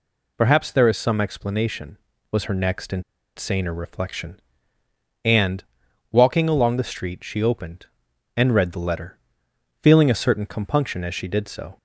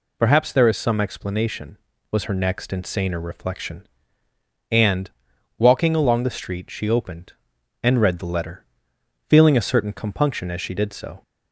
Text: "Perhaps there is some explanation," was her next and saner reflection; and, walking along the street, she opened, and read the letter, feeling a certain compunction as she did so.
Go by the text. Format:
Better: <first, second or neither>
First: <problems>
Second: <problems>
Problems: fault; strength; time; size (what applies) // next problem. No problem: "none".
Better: second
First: pauses between "and" and "saner"; at 3.0 s; 0.36 s long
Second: none